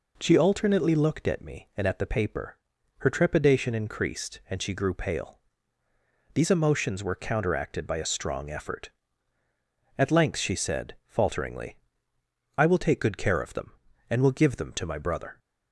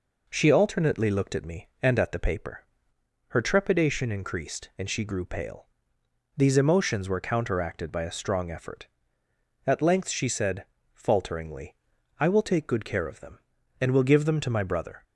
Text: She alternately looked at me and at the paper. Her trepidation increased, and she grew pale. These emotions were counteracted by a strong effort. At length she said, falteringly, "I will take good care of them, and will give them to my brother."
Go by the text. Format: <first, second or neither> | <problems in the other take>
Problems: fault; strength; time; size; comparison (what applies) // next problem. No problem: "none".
neither | none